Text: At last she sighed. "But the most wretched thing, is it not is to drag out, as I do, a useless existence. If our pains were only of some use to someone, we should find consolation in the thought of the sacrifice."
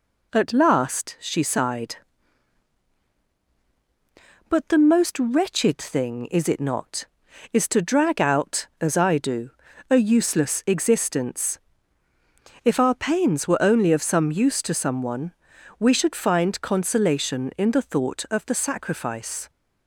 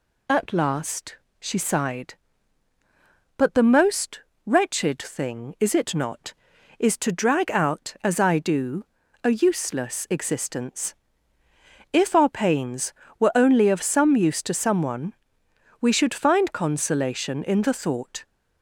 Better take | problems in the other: first | pauses between "last" and "she"; slight; at 1.1 s; 0.22 s long // pauses between "most" and "wretched"; slight; at 4.2 s; 0.26 s long // stops before "of the sacrifice"; at 18.2 s

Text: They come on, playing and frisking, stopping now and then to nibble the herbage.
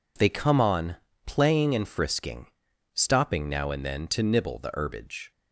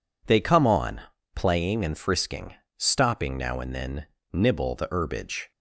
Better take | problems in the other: first | skips "to"; at 4.1 s

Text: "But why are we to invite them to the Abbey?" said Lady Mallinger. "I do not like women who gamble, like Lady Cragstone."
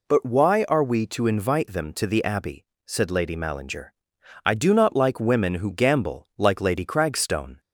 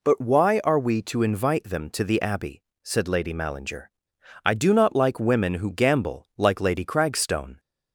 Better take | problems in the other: neither | none

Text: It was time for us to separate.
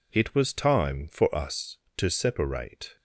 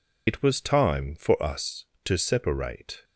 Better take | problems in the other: first | loses the start of "It"; at 0.2 s; 75 ms

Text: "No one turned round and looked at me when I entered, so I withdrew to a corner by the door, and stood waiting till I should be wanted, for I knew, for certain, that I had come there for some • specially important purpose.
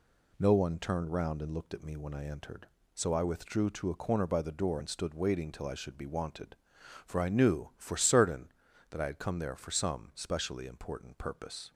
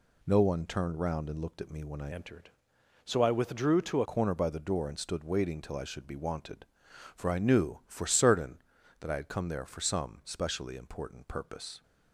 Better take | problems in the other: first | changes voice from "entered" to "a"; from 2.1 to 4.0 s; 1.9 s long

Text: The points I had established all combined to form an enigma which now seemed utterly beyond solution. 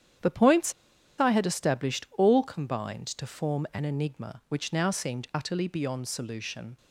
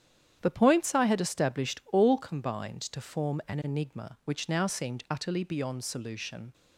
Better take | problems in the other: second | starts louder than the rest; strong; until 1.7 s; 9 dB; strong in the second // pauses between "points" and "I"; noticeable; at 0.7 s; 0.48 s long

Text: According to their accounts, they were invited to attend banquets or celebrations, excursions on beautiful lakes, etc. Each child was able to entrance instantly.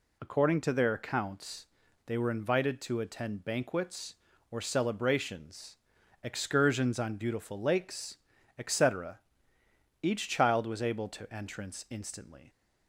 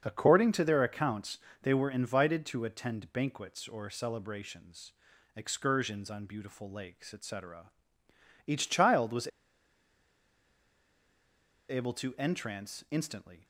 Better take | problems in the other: first | starts louder than the rest; until 1.0 s; 7 dB // pauses between "was" and "able"; strong; at 9.2 s; 2.4 s long

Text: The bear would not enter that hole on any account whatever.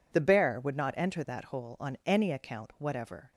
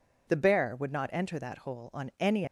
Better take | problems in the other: first | stops before "account whatever"; at 2.4 s

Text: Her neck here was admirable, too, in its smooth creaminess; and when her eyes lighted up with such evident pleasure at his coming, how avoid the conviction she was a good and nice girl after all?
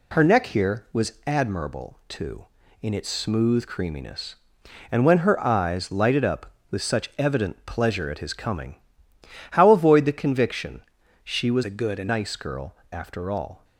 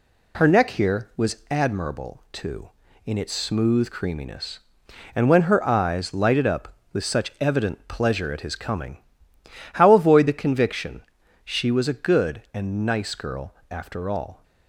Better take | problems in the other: second | pauses between "conviction" and "she"; at 10.8 s; 0.42 s long; also in the second // changes voice from "a" to "and"; from 11.6 to 12.0 s; 0.4 s long // pauses between "girl" and "after"; slight; at 12.7 s; 0.16 s long; slight in the second

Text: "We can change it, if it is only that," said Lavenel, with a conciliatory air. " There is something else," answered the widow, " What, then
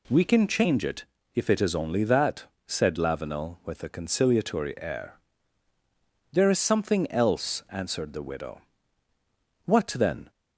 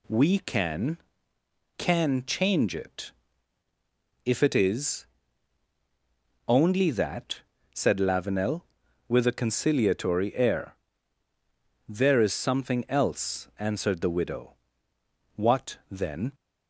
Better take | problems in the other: first | says "can" twice; at 1.7 s // pauses between "is" and "only"; strong; at 5.0 s; 1.4 s long

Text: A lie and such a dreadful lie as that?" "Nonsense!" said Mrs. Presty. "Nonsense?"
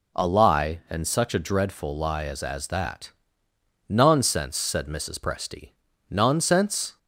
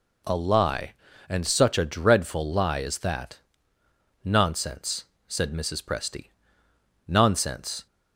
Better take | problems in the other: second | says "as" twice; at 2.4 s

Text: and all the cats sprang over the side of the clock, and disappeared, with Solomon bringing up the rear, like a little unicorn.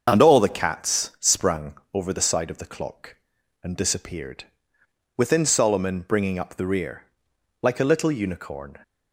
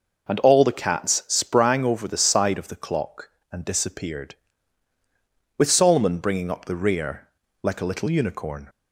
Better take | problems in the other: second | starts louder than the rest; until 1.2 s; 6.5 dB // pauses between "sprang" and "over"; slight; at 1.7 s; 0.18 s long // says "within" for "with"; at 5.1 s

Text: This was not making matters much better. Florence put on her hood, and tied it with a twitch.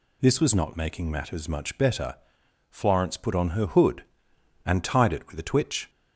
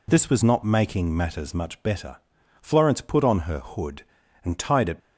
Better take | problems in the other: first | stops before "with a twitch"; at 4.9 s

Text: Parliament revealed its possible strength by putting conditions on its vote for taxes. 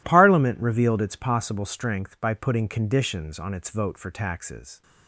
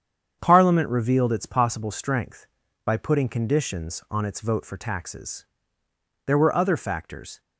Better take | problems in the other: first | starts louder than the rest; strong; until 1.4 s; 8 dB // goes on to say "There were other factors"; noticeable; from 6.2 s on; 1.1 s long

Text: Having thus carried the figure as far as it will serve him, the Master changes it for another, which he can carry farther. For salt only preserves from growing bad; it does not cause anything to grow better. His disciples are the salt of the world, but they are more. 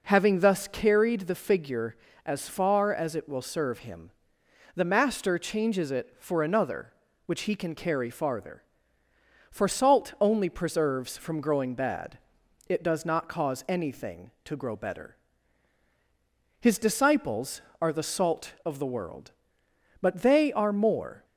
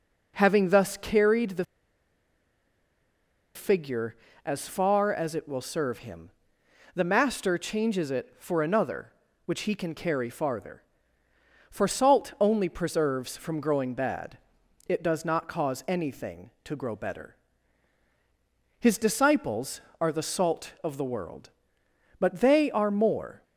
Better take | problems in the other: first | pauses between "the" and "figure"; strong; at 1.6 s; 1.9 s long

